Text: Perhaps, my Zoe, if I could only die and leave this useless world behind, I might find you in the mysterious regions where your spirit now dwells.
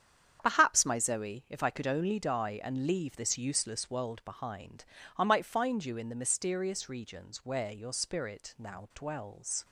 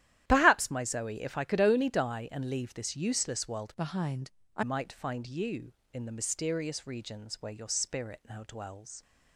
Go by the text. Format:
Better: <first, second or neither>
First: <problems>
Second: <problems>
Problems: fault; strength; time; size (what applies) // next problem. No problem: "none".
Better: first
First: starts louder than the rest; strong; until 1.4 s; 8.5 dB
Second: starts louder than the rest; strong; until 1.2 s; 12.5 dB // changes voice from "behind" to "I"; from 3.7 to 4.6 s; 0.9 s long